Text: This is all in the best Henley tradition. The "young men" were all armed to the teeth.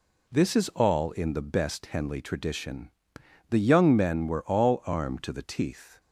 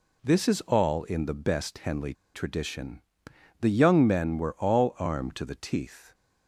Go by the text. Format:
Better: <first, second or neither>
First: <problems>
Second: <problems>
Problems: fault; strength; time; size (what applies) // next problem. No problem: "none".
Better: first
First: none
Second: pauses between "Henley" and "tradition"; slight; at 2.1 s; 0.20 s long